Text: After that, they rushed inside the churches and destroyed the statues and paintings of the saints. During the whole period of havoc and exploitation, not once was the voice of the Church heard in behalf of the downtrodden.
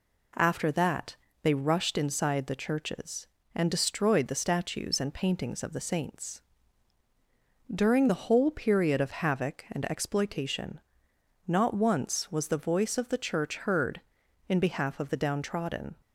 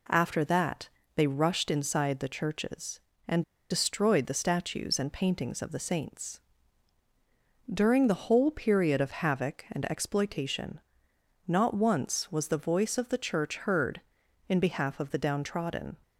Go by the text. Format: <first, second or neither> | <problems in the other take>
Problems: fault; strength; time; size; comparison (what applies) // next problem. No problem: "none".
first | pauses between "and" and "destroyed"; slight; at 3.4 s; 0.27 s long